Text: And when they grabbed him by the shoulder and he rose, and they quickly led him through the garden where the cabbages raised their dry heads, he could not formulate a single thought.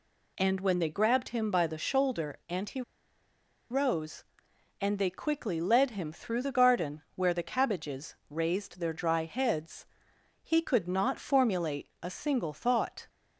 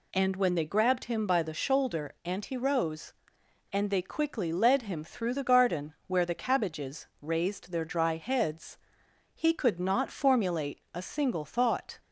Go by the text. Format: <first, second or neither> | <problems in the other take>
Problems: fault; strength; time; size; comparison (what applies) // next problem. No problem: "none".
second | pauses between "he" and "rose"; noticeable; at 2.8 s; 0.89 s long